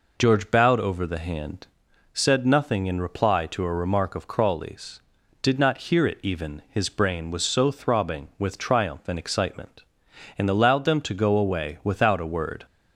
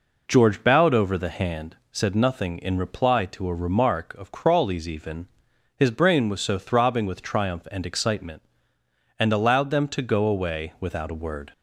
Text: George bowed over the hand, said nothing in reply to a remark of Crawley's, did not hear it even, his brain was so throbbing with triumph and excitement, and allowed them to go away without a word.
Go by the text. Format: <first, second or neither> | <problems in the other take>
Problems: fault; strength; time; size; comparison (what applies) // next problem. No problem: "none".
first | skips "did not hear it"; at 4.8 s